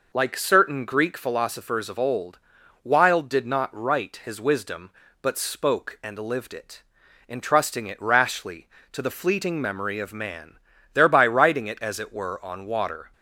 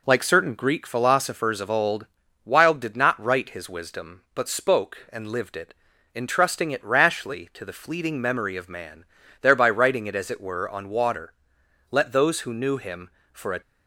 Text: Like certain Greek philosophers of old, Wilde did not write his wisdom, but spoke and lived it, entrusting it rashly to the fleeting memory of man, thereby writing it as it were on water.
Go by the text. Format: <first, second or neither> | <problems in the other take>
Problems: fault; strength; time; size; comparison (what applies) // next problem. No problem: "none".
first | goes on to say "Let those who knew him for a"; strong; from 11.8 s on; 1.7 s long